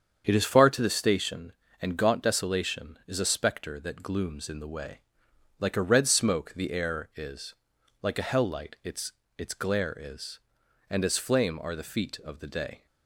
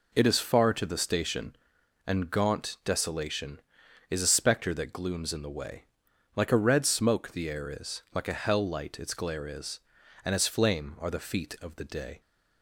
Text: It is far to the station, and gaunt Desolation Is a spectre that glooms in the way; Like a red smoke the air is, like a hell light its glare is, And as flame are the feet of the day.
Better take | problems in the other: second | starts louder than the rest; strong; until 1.2 s; 7.5 dB // says "its" twice; at 9.3 s

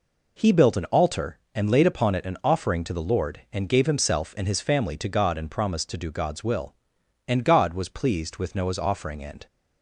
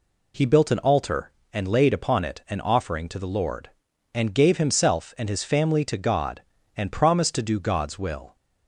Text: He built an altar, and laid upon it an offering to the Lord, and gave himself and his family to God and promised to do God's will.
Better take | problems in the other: second | goes on to say "And God was pleased with Noah's offering and"; strong; from 7.2 s on; 2.2 s long

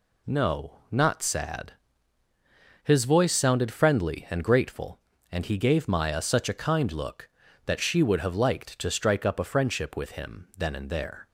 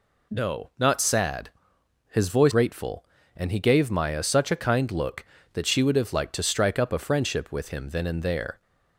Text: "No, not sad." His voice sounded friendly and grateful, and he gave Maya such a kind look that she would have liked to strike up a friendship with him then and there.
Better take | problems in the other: first | skips "sounded friendly and"; at 2.5 s

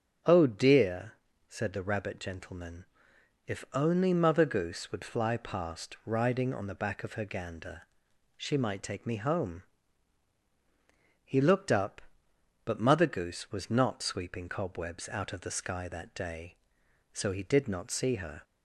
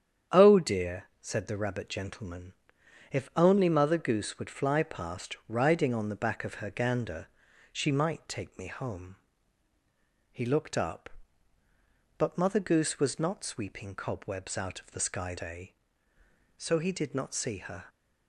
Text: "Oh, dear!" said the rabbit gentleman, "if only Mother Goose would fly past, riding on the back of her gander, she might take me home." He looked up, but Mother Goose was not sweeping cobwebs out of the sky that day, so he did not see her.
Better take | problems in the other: first | starts louder than the rest; strong; until 1.5 s; 8.5 dB; also in the first // skips "that"; at 15.3 s

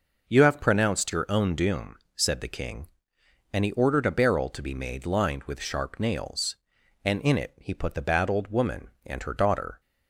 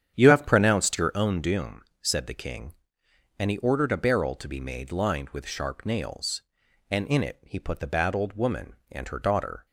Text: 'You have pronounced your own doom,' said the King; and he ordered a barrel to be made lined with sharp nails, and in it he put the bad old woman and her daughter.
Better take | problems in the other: first | starts louder than the rest; strong; until 1.2 s; 8.5 dB

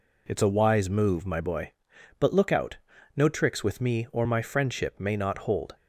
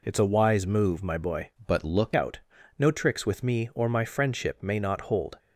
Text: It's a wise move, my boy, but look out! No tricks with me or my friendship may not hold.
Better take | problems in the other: first | changes voice from "but" to "look"; from 1.6 to 2.1 s; 0.5 s long

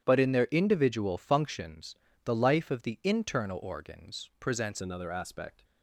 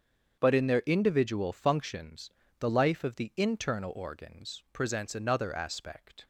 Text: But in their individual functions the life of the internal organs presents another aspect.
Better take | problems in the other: second | starts louder than the rest; strong; until 1.0 s; 10 dB; strong in the second // pauses between "functions" and "the"; slight; at 1.9 s; 0.30 s long; slight in the second // changes voice at "another"; from 4.7 s on; 0.9 s long

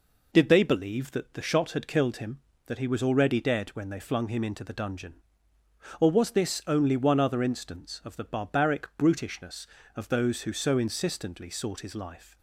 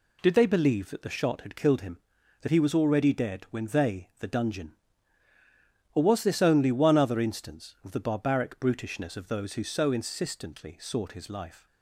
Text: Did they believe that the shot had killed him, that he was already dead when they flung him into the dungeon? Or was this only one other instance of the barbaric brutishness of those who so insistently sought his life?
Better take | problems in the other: first | skips "flung him into"; at 4.1 s

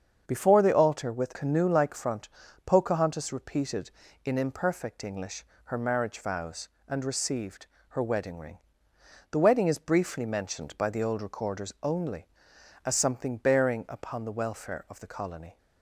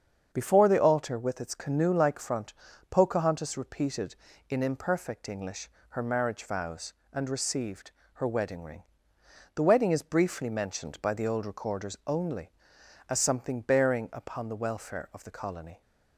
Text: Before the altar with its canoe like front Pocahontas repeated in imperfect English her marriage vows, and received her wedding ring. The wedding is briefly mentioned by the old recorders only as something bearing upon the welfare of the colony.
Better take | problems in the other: second | starts louder than the rest; strong; until 1.2 s; 7 dB; strong in the second // skips "its"; at 1.3 s // pauses between "front" and "Pocahontas"; slight; at 2.2 s; 0.36 s long; slight in the second // pauses between "English" and "her"; slight; at 5.4 s; 0.22 s long; slight in the second // pauses between "received" and "her"; slight; at 7.6 s; 0.22 s long; slight in the second

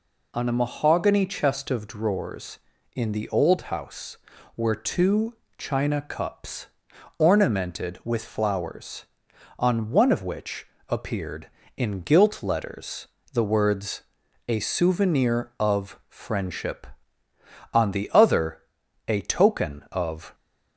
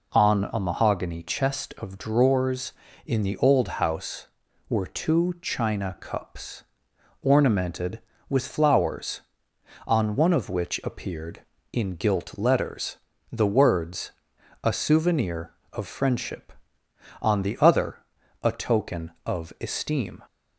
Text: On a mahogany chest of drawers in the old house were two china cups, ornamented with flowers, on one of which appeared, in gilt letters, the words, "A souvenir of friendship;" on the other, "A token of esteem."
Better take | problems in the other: second | pauses between "two" and "china"; slight; at 5.3 s; 0.24 s long // pauses between "which" and "appeared"; slight; at 10.6 s; 0.20 s long // stops before "esteem"; at 20.3 s

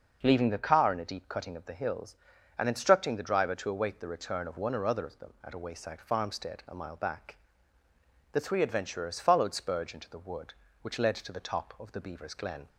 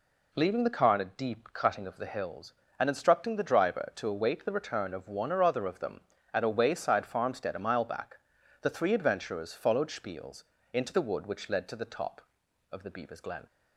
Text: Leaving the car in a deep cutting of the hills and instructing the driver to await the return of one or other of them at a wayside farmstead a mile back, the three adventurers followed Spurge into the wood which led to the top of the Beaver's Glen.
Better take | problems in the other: first | says "Spiels" for "Spurge"; at 9.8 s

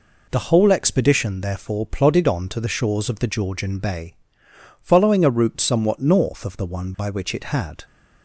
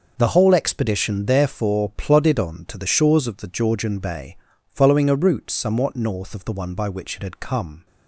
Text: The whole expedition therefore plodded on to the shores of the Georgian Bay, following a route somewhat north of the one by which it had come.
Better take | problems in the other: second | stops before "come"; at 7.8 s

